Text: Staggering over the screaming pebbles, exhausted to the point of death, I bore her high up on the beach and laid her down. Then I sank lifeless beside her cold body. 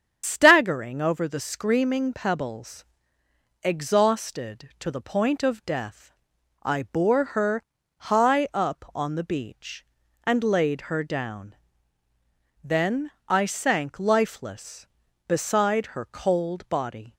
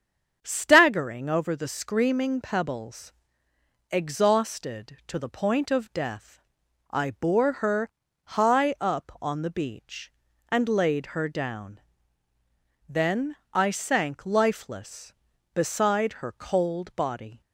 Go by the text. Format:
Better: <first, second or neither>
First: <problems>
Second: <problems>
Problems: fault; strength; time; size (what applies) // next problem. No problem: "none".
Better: second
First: loses the start of "Staggering"; at 0.2 s; 95 ms // starts louder than the rest; strong; until 1.2 s; 8 dB // pauses between "her" and "high"; slight; at 7.6 s; 0.34 s long // pauses between "Then" and "I"; slight; at 13.0 s; 0.20 s long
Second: starts louder than the rest; strong; until 1.4 s; 7.5 dB // pauses between "her" and "high"; slight; at 7.9 s; 0.34 s long // pauses between "Then" and "I"; slight; at 13.3 s; 0.20 s long